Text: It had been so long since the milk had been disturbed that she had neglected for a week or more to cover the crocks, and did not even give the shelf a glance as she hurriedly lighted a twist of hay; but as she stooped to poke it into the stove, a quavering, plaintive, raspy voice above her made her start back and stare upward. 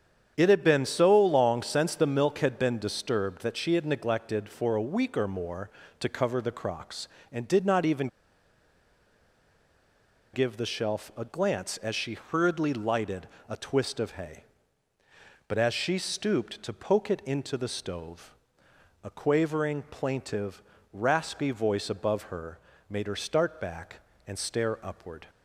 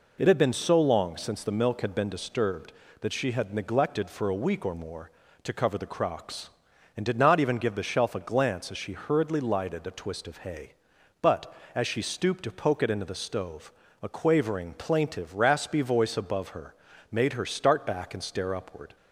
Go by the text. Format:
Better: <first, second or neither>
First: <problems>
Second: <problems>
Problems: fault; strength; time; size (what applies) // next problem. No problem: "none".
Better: second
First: starts louder than the rest; strong; until 1.3 s; 8.5 dB // pauses between "even" and "give"; strong; at 8.0 s; 2.2 s long // pauses between "lighted" and "a"; slight; at 13.2 s; 0.22 s long // pauses between "her" and "made"; slight; at 22.6 s; 0.28 s long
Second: pauses between "her" and "made"; at 16.7 s; 0.38 s long